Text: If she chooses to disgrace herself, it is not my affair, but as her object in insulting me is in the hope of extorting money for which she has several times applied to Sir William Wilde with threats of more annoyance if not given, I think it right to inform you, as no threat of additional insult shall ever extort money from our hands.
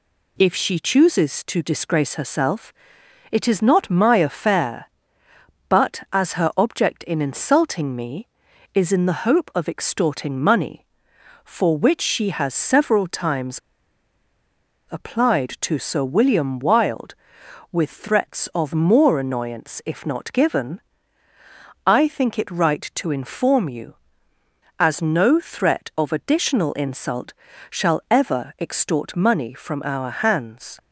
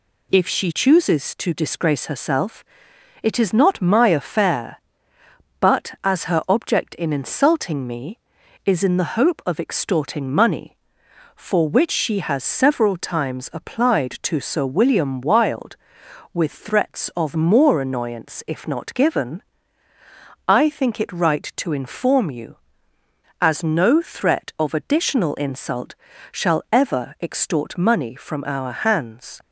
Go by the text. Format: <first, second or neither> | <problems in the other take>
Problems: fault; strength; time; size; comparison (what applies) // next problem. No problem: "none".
second | pauses between "times" and "applied"; strong; at 13.5 s; 1.3 s long // pauses between "insult" and "shall"; slight; at 27.3 s; 0.36 s long; slight in the second